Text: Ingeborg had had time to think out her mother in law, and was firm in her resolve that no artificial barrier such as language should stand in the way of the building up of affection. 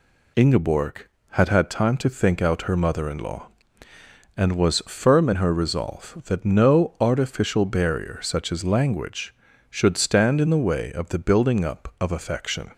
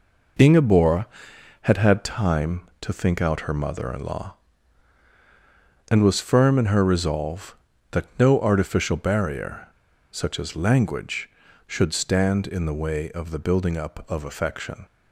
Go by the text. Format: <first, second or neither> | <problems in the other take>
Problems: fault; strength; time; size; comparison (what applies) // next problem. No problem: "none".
first | pauses between "barrier" and "such"; at 9.6 s; 0.43 s long